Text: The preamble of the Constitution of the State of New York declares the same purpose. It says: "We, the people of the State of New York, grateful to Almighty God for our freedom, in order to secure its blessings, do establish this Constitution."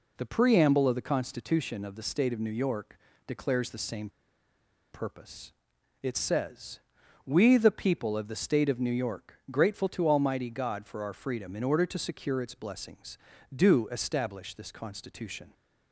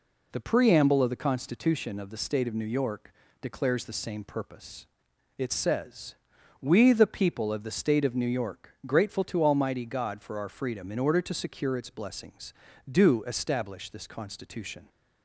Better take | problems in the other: second | pauses between "York" and "declares"; slight; at 2.9 s; 0.30 s long; slight in the second // pauses between "same" and "purpose"; noticeable; at 4.0 s; 0.83 s long

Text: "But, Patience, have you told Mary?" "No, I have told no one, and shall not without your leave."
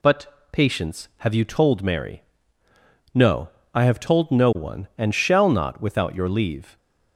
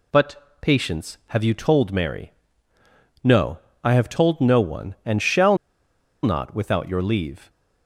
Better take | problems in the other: first | pauses between "shall" and "not"; noticeable; at 5.5 s; 0.67 s long

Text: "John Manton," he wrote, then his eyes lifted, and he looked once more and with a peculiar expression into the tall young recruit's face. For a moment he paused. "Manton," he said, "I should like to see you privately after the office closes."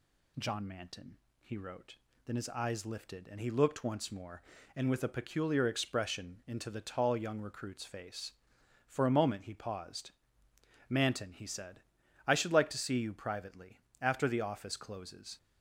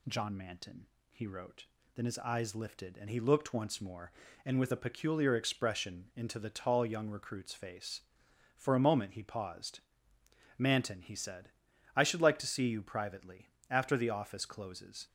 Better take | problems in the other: neither | pauses between "privately" and "after"; slight; the same in both

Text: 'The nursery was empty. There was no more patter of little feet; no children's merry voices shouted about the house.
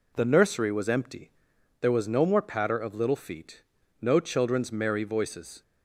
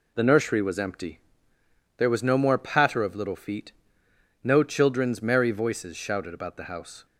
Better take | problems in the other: second | stops before "shouted about the house"; at 5.6 s

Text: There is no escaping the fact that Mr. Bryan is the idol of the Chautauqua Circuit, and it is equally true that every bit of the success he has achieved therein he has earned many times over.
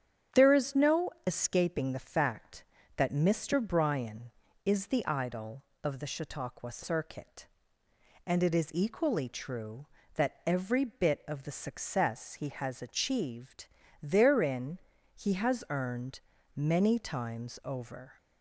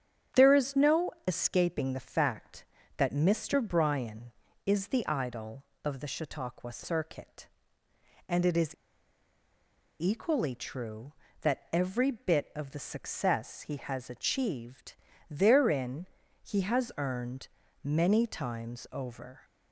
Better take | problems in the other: first | starts louder than the rest; strong; until 1.5 s; 9 dB; strong in the first // pauses between "no" and "escaping"; slight; at 1.1 s; 0.16 s long; slight in the first // pauses between "is" and "equally"; strong; at 8.7 s; 1.2 s long // pauses between "achieved" and "therein"; slight; at 14.9 s; 0.36 s long; slight in the first // pauses between "therein" and "he"; slight; at 16.0 s; 0.36 s long; slight in the first // pauses between "earned" and "many"; at 17.4 s; 0.38 s long; also in the first

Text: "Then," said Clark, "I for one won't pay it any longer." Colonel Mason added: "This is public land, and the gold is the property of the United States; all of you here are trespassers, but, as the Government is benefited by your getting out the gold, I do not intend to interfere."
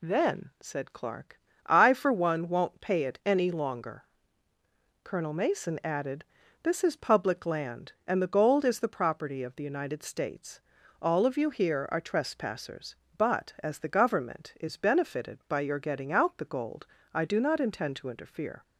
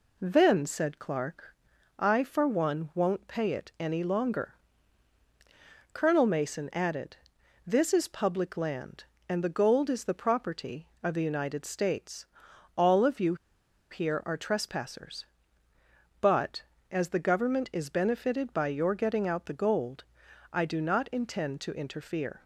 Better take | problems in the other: first | pauses between "you" and "here"; noticeable; at 13.3 s; 0.55 s long

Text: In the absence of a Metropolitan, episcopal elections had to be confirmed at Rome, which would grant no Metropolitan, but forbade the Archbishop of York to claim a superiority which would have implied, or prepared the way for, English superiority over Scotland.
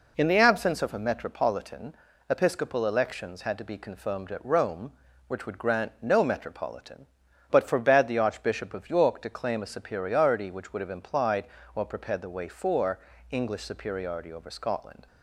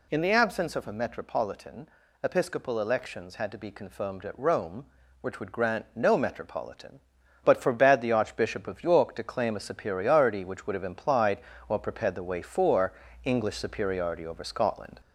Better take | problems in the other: first | gets louder; slight; throughout; 3 dB

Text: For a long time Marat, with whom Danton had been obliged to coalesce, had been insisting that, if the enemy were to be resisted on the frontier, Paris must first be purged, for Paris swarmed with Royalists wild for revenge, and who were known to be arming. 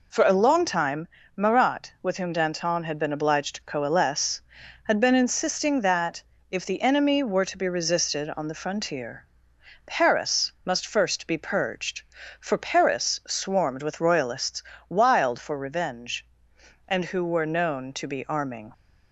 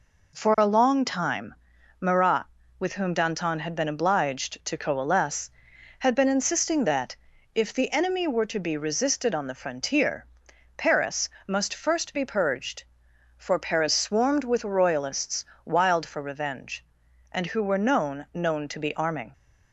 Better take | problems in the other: first | pauses between "time" and "Marat"; at 1.5 s; 0.44 s long; slight in the first // pauses between "Paris" and "must"; slight; at 11.3 s; 0.18 s long // pauses between "Royalists" and "wild"; slight; at 15.4 s; 0.22 s long; slight in the first // says "known" twice; at 18.3 s

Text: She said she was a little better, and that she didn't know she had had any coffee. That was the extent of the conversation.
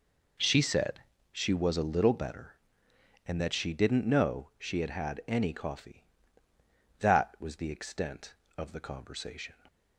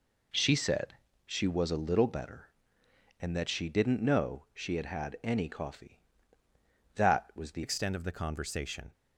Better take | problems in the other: first | pauses between "said" and "she"; slight; at 0.9 s; 0.32 s long; slight in the first // changes voice at "extent"; from 7.6 s on; 1.3 s long

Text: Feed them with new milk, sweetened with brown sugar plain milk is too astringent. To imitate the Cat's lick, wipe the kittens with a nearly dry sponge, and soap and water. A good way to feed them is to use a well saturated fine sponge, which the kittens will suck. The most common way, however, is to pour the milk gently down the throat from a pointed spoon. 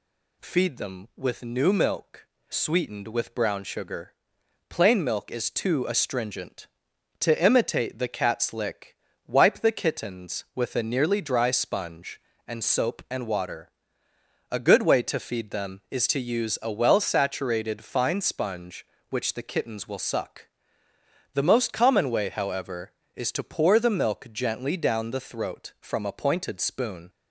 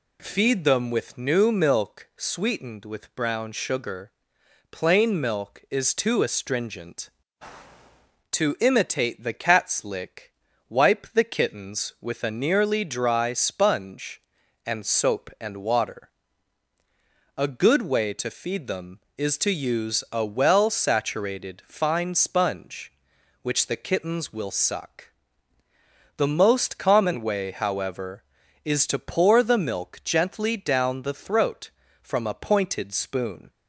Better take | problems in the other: neither | pauses between "sugar" and "plain"; noticeable; the same in both

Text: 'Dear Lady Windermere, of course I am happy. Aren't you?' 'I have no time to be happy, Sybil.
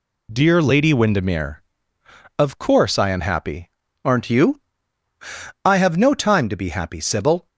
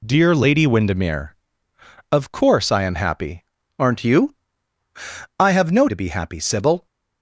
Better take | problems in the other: first | skips "time"; at 5.8 s

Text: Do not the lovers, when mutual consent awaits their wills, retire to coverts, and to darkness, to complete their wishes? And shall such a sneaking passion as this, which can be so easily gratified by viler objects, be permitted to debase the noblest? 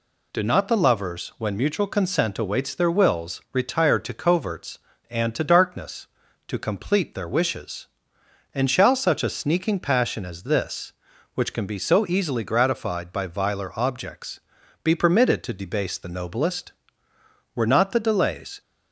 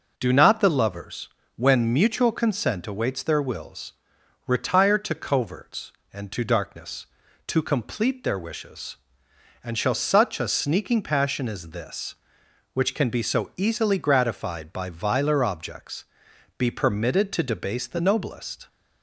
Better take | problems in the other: second | goes on to say "Were not the delays"; noticeable; from 17.5 s on; 1.0 s long

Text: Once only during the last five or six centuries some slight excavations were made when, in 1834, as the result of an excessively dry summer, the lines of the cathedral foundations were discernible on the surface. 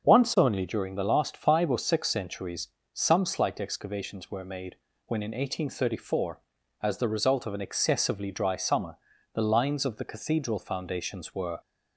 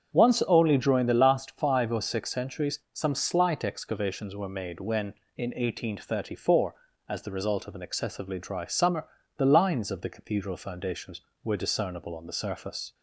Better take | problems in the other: second | starts louder than the rest; until 1.0 s; 6.5 dB; also in the second // pauses between "centuries" and "some"; slight; at 2.6 s; 0.24 s long; slight in the second // pauses between "made" and "when"; slight; at 4.7 s; 0.32 s long // stops before "discernible on the surface"; at 11.6 s

